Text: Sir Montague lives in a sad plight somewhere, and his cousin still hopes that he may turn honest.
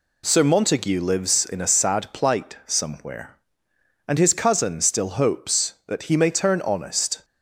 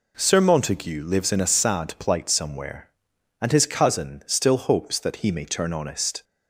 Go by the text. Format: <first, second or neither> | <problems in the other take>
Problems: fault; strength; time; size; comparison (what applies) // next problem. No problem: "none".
neither | none